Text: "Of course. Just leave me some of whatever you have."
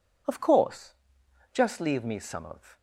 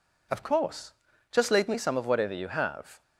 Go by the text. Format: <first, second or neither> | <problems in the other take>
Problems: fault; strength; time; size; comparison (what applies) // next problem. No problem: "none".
second | stops before "whatever you have"; at 2.7 s